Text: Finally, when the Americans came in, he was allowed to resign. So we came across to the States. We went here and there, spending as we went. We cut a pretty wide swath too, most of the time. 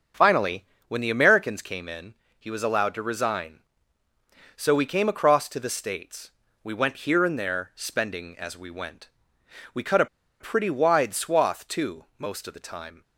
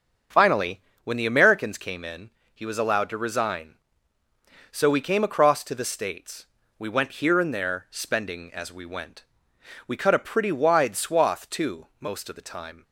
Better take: second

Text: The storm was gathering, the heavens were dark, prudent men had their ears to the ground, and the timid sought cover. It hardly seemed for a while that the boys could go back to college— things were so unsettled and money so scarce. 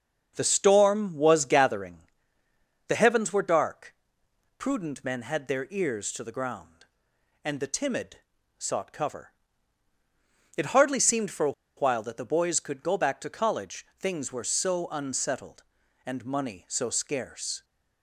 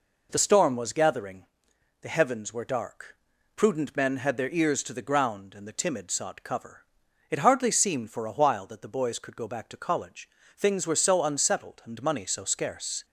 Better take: second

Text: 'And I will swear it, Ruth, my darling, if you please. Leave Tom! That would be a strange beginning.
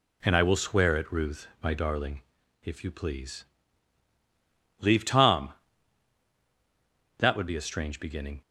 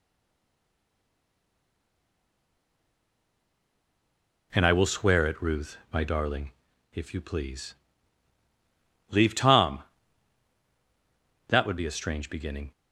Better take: first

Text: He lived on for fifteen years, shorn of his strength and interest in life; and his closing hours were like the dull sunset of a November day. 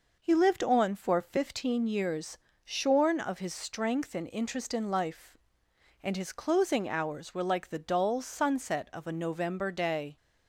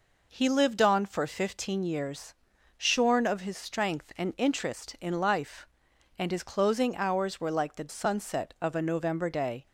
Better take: first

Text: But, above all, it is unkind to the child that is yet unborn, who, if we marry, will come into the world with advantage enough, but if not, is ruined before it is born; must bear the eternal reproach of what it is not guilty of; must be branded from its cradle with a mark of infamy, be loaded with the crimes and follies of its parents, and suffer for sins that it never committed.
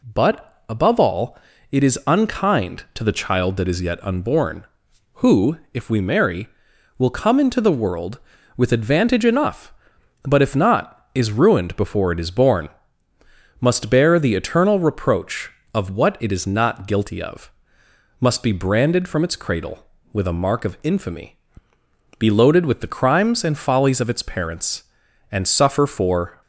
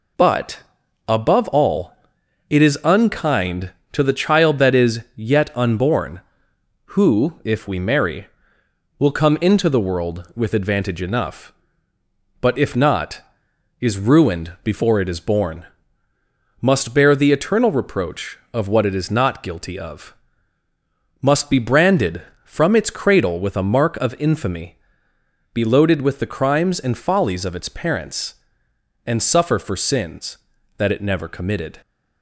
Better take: second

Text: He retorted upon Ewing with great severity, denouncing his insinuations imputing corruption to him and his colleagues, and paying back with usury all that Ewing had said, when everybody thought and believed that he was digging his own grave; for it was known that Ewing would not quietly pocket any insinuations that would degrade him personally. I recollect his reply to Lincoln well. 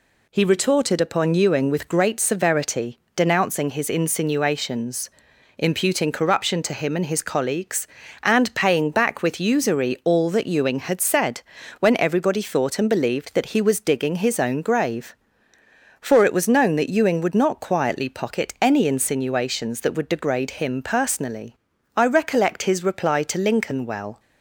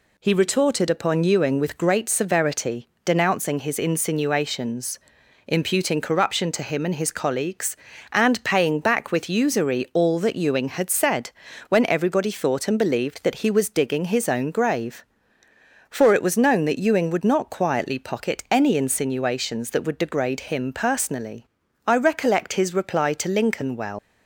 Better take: first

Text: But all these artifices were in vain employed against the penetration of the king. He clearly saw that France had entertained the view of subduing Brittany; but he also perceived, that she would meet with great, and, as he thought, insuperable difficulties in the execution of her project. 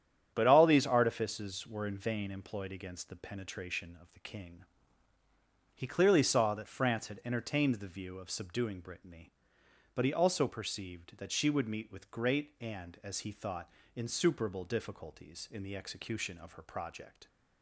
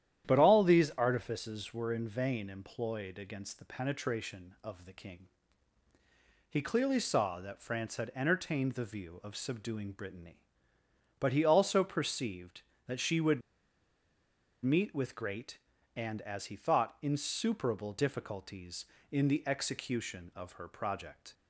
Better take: first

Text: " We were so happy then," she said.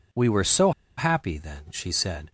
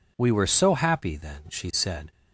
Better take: second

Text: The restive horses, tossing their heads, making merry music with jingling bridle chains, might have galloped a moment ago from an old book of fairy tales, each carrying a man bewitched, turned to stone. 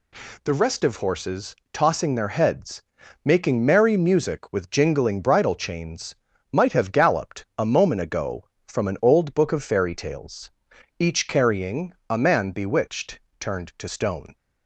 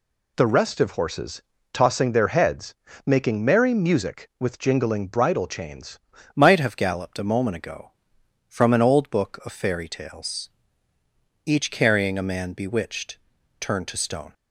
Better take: first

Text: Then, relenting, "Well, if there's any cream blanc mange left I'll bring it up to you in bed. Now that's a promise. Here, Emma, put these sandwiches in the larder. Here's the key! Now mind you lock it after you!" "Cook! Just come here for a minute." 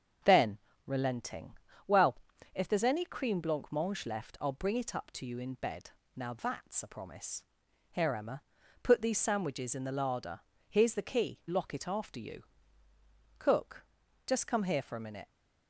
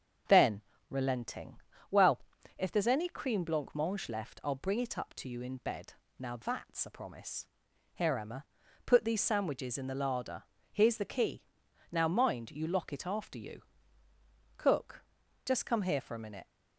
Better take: second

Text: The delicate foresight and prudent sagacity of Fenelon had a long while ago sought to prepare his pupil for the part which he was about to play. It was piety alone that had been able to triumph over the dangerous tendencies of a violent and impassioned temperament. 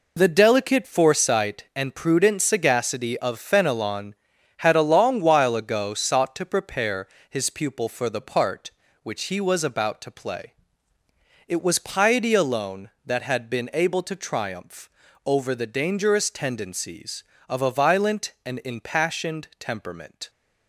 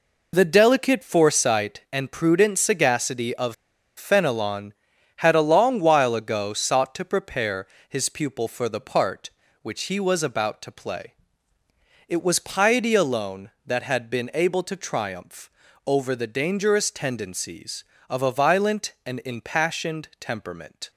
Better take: first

